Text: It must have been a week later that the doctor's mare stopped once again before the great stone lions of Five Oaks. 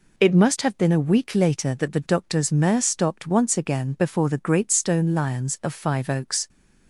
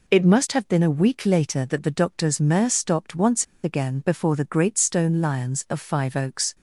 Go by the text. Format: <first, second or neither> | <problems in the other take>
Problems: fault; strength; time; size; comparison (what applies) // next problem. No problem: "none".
first | pauses between "once" and "again"; slight; at 3.4 s; 0.18 s long